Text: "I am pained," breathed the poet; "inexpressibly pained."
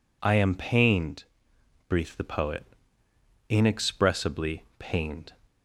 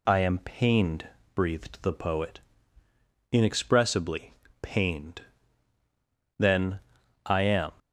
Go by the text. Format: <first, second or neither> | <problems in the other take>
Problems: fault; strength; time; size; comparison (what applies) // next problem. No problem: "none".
first | pauses between "inexpressibly" and "pained"; slight; at 4.3 s; 0.28 s long; slight in the first // goes on to say "Then I am"; from 6.3 s on; 1.3 s long